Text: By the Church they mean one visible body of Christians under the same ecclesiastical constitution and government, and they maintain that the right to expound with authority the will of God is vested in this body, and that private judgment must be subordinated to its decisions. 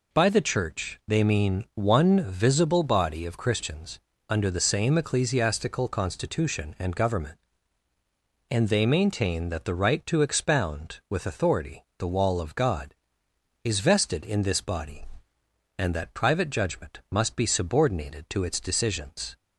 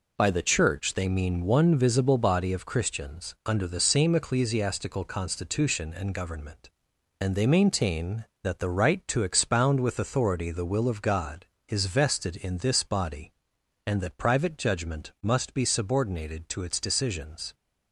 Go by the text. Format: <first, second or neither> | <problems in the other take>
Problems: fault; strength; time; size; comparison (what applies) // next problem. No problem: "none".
second | pauses between "Christians" and "under"; slight; at 4.0 s; 0.28 s long // says "wall" for "will"; at 12.0 s